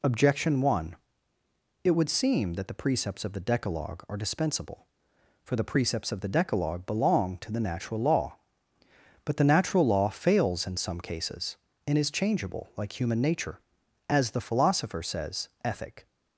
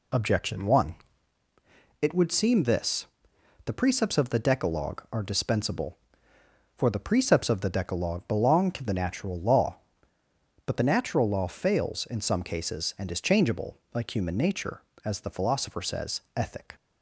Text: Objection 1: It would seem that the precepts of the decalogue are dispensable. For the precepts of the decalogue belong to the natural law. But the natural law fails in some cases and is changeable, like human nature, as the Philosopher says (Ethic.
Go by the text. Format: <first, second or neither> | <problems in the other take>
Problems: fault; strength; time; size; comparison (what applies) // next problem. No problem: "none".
first | says "this" for "that"; at 2.6 s